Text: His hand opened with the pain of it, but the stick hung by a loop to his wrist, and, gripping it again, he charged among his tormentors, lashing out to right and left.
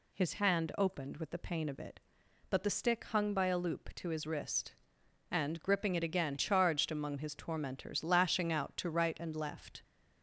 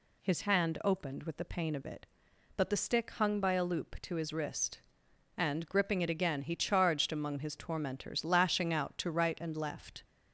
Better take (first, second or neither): second